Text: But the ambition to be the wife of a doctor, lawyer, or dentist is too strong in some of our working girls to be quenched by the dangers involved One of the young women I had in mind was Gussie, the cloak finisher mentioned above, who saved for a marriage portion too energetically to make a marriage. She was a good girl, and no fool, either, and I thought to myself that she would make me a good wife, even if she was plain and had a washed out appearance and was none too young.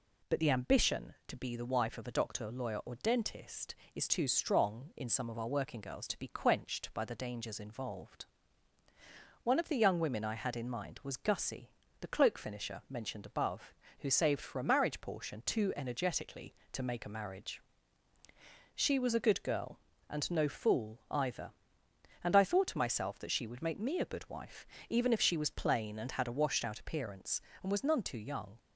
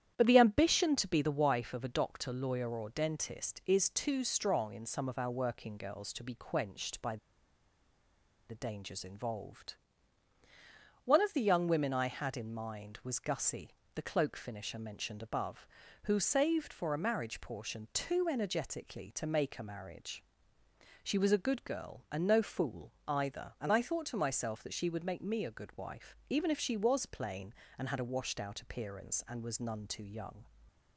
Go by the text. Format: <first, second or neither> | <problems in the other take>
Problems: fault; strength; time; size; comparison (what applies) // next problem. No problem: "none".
first | starts louder than the rest; strong; until 1.1 s; 10 dB // pauses between "by" and "the"; strong; at 7.1 s; 1.3 s long // pauses between "involved" and "One"; strong; at 9.7 s; 1.3 s long; also in the first